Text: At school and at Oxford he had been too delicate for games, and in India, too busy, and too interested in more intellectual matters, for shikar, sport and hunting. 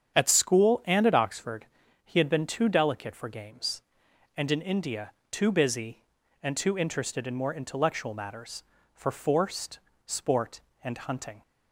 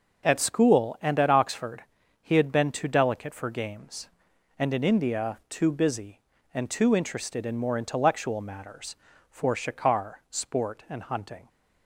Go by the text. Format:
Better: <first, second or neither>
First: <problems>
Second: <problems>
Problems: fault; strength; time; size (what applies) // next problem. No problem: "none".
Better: second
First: starts louder than the rest; strong; until 1.2 s; 8.5 dB // pauses between "Oxford" and "he"; at 1.6 s; 0.38 s long // says "forced" for "shikar"; at 9.1 s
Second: pauses between "Oxford" and "he"; at 1.8 s; 0.40 s long